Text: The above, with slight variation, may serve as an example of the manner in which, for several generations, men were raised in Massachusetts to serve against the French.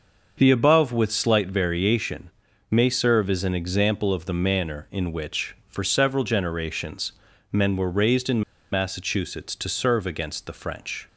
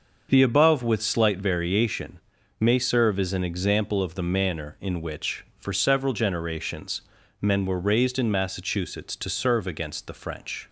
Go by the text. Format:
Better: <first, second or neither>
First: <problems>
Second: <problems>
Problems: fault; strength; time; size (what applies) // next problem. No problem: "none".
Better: second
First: starts louder than the rest; until 1.3 s; 6.5 dB // pauses between "in" and "Massachusetts"; slight; at 8.4 s; 0.31 s long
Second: starts louder than the rest; until 1.3 s; 6.5 dB